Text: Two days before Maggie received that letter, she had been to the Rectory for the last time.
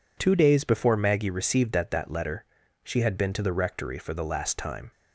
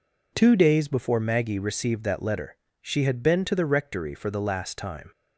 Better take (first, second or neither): second